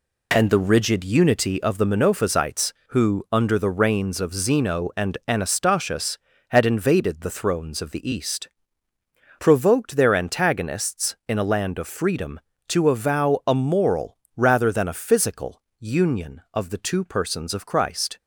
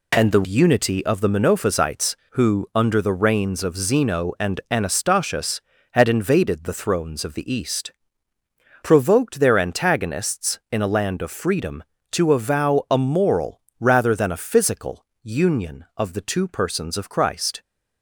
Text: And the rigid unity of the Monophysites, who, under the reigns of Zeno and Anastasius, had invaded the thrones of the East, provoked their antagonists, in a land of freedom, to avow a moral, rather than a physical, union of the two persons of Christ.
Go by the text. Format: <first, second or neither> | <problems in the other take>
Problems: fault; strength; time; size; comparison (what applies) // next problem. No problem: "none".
first | skips "rigid"; at 0.4 s